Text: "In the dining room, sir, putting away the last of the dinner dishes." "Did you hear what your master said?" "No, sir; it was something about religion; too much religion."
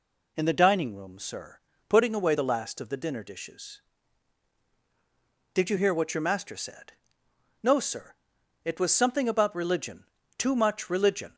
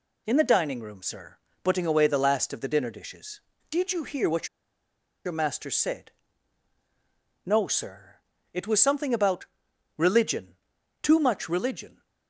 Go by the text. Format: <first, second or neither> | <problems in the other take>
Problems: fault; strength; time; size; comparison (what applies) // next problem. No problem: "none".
first | pauses between "what" and "your"; noticeable; at 4.4 s; 0.78 s long // pauses between "about" and "religion"; noticeable; at 9.4 s; 0.50 s long